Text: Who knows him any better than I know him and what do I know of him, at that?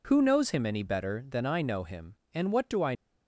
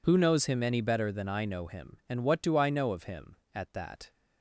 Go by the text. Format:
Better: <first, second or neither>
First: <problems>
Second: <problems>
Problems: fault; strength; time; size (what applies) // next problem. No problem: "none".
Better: second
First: stops before "know of him at that"; at 2.9 s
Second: none